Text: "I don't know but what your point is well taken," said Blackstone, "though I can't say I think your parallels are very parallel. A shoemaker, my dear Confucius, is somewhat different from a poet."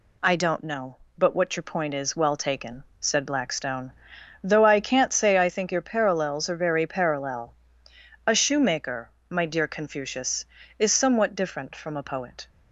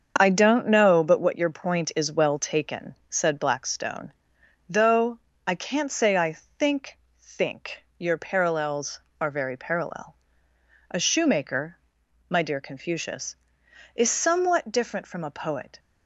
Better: first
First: none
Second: starts louder than the rest; until 1.1 s; 7 dB // pauses between "though" and "I"; slight; at 5.1 s; 0.28 s long // pauses between "I" and "think"; slight; at 6.3 s; 0.24 s long // says "think" twice; at 7.2 s

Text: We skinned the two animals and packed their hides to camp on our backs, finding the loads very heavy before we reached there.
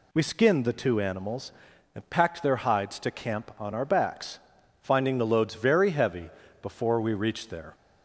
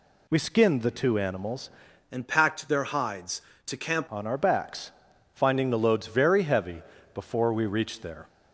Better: first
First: pauses between "heavy" and "before"; slight; at 6.3 s; 0.32 s long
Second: changes voice from "and" to "camp"; from 2.1 to 4.0 s; 1.9 s long // pauses between "heavy" and "before"; slight; at 6.8 s; 0.32 s long

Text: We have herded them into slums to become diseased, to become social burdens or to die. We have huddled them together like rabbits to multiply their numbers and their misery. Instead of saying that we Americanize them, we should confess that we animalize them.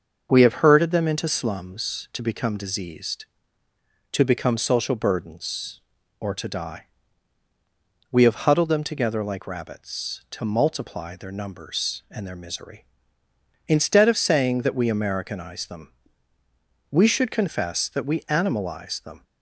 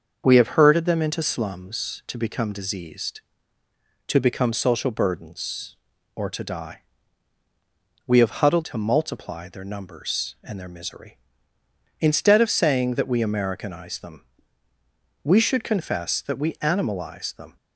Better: first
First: starts louder than the rest; until 1.3 s; 6.5 dB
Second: starts louder than the rest; until 1.2 s; 6.5 dB // skips "them together like rabbits"; at 8.6 s

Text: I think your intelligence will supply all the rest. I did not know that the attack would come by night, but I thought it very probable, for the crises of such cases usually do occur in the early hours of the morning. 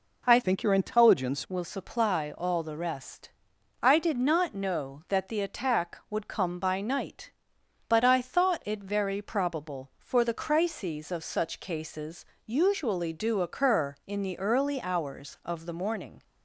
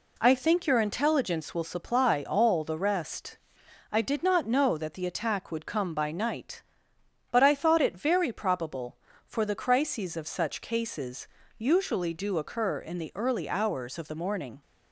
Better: second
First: changes voice from "think" to "intelligence"; from 0.4 to 1.4 s; 1.0 s long // pauses between "cases" and "usually"; slight; at 12.2 s; 0.22 s long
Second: pauses between "cases" and "usually"; slight; at 11.2 s; 0.32 s long

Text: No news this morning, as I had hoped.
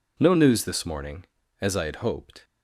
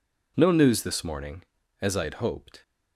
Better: neither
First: none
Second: none

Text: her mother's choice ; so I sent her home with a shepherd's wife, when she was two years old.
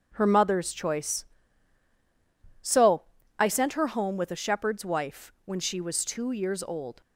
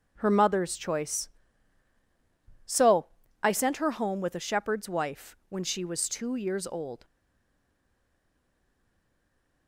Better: first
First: pauses between "so" and "I"; slight; at 3.0 s; 0.34 s long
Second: pauses between "so" and "I"; slight; at 3.0 s; 0.34 s long // stays silent after the last word; strong; from 7.0 s on; 2.6 s long

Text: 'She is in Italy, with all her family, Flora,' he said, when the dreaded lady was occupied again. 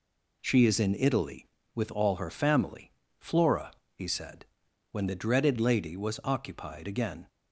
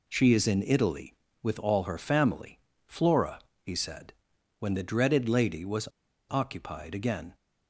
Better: first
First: none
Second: pauses between "was" and "occupied"; at 5.8 s; 0.40 s long

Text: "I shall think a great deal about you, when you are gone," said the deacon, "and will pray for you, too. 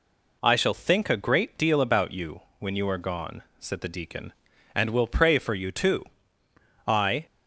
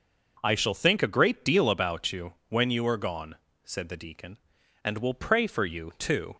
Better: second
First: goes on to say "I"; slight; from 6.8 s on; 0.38 s long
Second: none

